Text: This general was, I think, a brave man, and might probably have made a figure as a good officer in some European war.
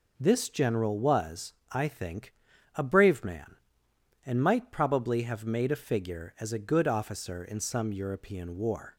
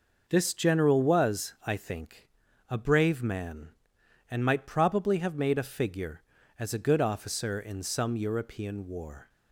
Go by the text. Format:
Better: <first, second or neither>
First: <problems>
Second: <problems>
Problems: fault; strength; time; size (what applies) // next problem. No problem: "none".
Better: neither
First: none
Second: none